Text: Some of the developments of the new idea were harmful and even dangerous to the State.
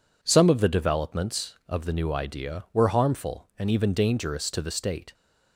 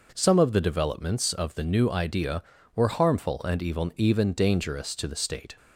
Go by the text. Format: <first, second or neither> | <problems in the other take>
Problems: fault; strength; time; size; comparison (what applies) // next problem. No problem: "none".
first | says "even" twice; at 3.9 s